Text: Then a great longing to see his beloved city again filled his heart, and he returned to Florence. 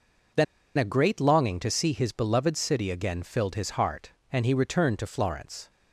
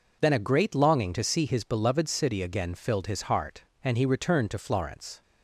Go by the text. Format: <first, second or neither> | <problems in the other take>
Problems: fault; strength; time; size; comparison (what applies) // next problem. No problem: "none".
second | pauses between "Then" and "a"; slight; at 0.4 s; 0.33 s long